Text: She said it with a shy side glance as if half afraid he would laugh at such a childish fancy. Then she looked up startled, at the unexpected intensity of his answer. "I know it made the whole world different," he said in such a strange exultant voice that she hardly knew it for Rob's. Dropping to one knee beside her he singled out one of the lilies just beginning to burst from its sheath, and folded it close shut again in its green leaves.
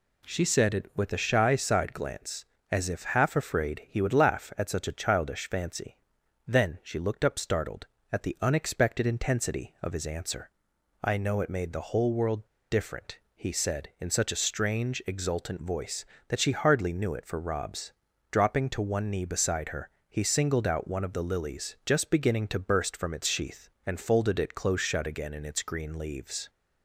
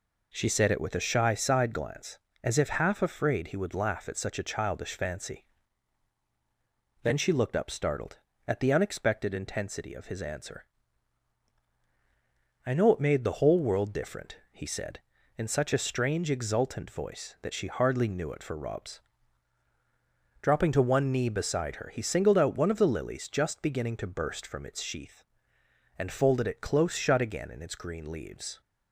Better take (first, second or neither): second